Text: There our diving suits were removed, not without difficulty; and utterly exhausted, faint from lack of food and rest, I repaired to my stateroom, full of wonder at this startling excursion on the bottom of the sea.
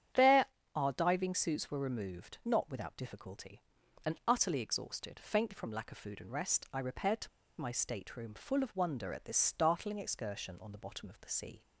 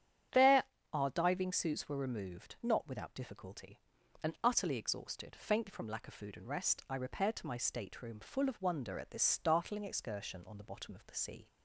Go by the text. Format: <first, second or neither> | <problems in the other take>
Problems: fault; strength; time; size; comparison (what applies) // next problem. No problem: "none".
second | starts louder than the rest; strong; until 1.4 s; 9.5 dB; strong in the second // pauses between "There" and "our"; slight; at 0.4 s; 0.32 s long; slight in the second // pauses between "to" and "my"; slight; at 7.2 s; 0.32 s long